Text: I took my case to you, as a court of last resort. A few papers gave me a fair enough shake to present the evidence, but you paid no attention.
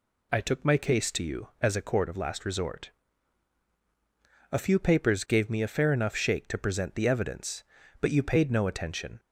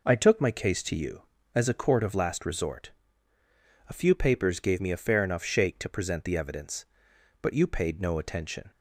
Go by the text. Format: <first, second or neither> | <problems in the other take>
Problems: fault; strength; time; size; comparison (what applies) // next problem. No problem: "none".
neither | none